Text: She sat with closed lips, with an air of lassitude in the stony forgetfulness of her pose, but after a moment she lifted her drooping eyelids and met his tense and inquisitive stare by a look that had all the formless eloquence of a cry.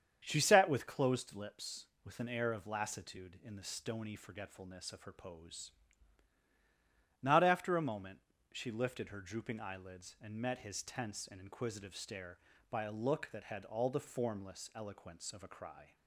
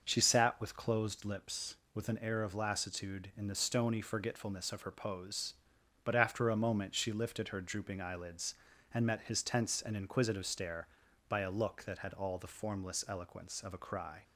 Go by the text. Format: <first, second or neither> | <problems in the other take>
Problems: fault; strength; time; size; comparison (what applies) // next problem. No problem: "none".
second | starts louder than the rest; strong; until 1.2 s; 8 dB; noticeable in the second // says "not" for "but"; at 7.2 s // pauses between "moment" and "she"; slight; at 8.1 s; 0.34 s long